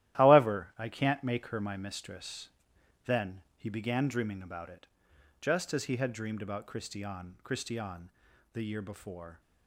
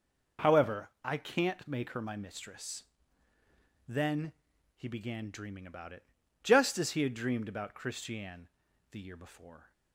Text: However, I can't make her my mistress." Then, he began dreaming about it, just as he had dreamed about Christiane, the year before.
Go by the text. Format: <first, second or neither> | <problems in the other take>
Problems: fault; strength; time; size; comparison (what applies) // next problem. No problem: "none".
second | starts louder than the rest; strong; until 1.2 s; 13.5 dB // says "Christiane" twice; at 7.4 s